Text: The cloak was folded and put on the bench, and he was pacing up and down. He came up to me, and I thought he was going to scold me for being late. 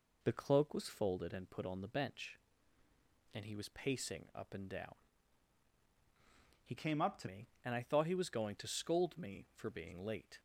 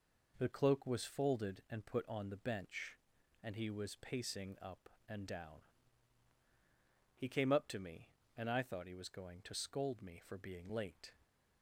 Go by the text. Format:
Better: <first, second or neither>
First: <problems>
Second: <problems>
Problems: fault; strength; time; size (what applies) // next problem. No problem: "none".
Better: second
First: changes voice from "came" to "to"; from 6.7 to 7.2 s; 0.5 s long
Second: none